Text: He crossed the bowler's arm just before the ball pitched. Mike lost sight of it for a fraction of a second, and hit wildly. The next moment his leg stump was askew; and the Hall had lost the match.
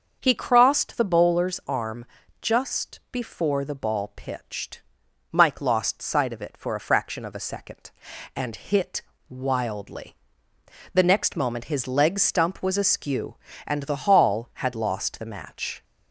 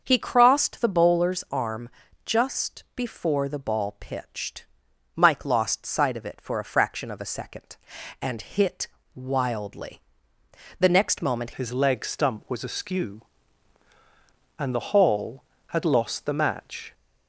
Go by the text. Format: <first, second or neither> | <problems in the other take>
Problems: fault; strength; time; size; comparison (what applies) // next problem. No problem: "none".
first | starts louder than the rest; until 1.0 s; 6.5 dB; also in the first // pauses between "arm" and "just"; slight; at 1.8 s; 0.36 s long; slight in the first // pauses between "hit" and "wildly"; slight; at 8.8 s; 0.28 s long; slight in the first // changes voice at "his"; from 11.5 s on; 5.4 s long